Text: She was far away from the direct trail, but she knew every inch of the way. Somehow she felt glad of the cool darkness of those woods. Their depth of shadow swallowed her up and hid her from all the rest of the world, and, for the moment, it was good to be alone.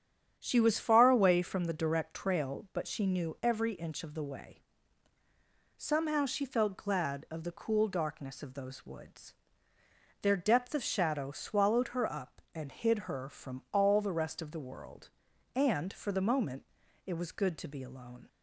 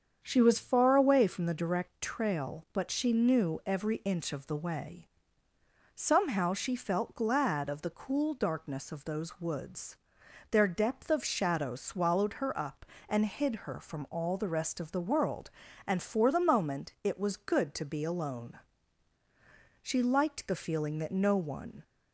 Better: first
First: starts louder than the rest; strong; until 1.4 s; 8.5 dB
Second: starts louder than the rest; strong; until 1.2 s; 7.5 dB // goes on to say "She liked the feeling that no one"; strong; from 19.8 s on; 2.0 s long

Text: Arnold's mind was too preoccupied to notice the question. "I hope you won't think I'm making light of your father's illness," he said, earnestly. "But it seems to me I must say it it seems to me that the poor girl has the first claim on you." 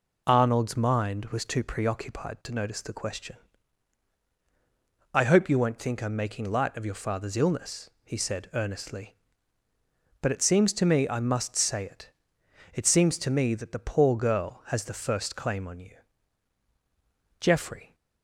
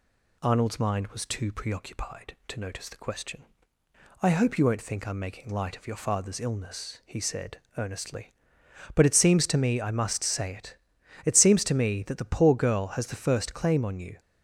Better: second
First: pauses between "it" and "it"; noticeable; at 12.1 s; 0.64 s long // goes on to say "Geoffrey"; from 17.3 s on; 0.56 s long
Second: pauses between "it" and "it"; noticeable; at 10.7 s; 0.50 s long

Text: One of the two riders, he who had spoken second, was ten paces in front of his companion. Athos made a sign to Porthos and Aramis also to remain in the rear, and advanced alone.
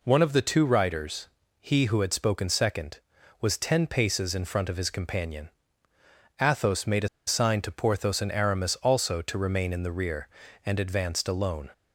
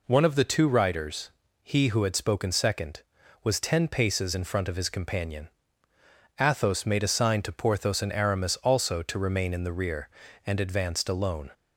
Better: second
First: pauses between "a" and "sign"; slight; at 7.0 s; 0.19 s long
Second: none

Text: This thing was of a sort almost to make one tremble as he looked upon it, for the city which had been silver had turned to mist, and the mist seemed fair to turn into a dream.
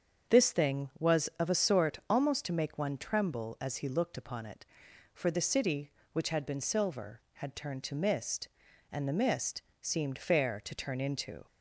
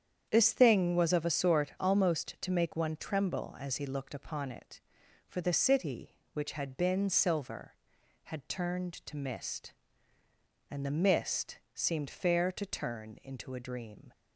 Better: second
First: starts louder than the rest; strong; until 1.5 s; 7 dB // pauses between "mist" and "seemed"; slight; at 9.6 s; 0.18 s long // stops before "a dream"; at 11.4 s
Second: starts louder than the rest; strong; until 1.3 s; 8.5 dB

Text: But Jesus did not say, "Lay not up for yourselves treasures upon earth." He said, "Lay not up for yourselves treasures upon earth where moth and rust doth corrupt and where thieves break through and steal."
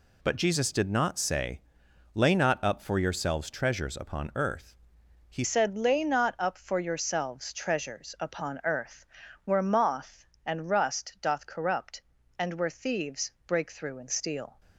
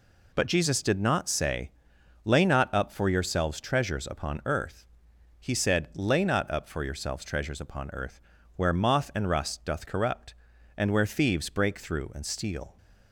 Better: second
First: changes voice at "said"; from 5.4 s on; 9.1 s long // pauses between "earth" and "where"; at 9.0 s; 0.40 s long // pauses between "thieves" and "break"; slight; at 13.3 s; 0.16 s long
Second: pauses between "earth" and "where"; slight; at 8.2 s; 0.34 s long

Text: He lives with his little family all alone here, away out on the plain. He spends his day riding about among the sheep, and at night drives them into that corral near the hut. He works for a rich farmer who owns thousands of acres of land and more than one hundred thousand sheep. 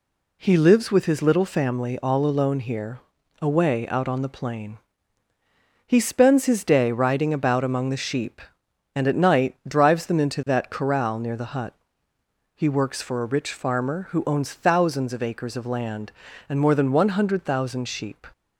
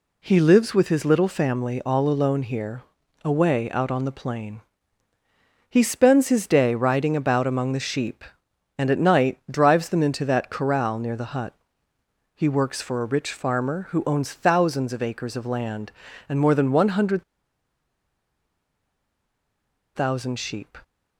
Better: first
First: none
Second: pauses between "hundred" and "thousand"; strong; at 17.2 s; 2.7 s long

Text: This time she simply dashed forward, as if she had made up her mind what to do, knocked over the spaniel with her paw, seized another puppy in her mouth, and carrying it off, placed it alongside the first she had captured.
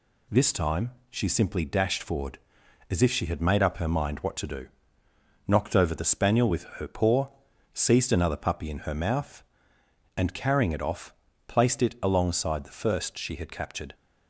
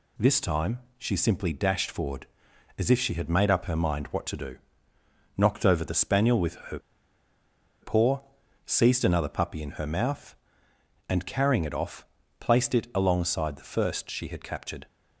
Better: first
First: pauses between "time" and "she"; slight; at 0.9 s; 0.18 s long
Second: pauses between "time" and "she"; slight; at 0.7 s; 0.18 s long // pauses between "her" and "paw"; at 6.7 s; 1.0 s long

